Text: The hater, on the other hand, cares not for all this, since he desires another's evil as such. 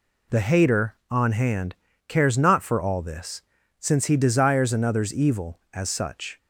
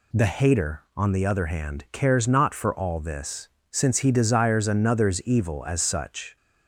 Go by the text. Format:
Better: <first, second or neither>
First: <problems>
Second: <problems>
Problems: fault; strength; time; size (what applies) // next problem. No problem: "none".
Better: second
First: skips "the other"; at 1.3 s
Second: none